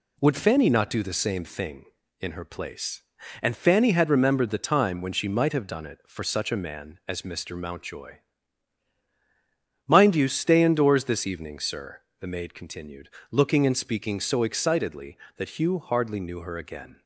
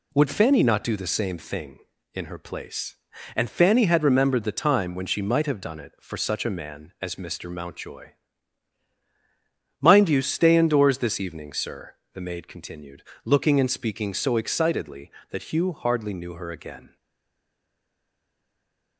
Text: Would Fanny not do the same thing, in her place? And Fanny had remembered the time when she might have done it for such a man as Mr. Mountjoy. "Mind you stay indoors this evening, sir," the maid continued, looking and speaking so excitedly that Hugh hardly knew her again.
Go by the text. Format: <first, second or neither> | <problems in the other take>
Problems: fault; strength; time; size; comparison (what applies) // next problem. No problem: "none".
first | stays silent after the last word; from 16.9 s on; 2.0 s long